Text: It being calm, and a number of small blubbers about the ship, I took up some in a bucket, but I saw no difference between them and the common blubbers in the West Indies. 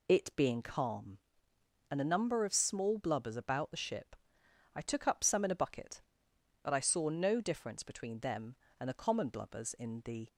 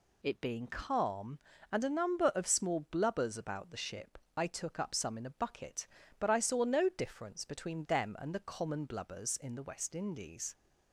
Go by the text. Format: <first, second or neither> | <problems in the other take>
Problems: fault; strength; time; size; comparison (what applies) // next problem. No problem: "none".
second | stops before "West Indies"; at 10.2 s